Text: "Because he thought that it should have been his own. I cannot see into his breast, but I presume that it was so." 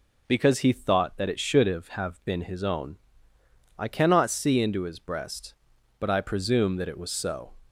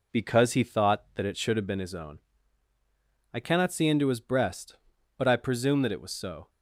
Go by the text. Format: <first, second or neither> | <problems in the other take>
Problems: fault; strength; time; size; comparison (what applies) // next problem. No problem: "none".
second | says "have" twice; at 1.8 s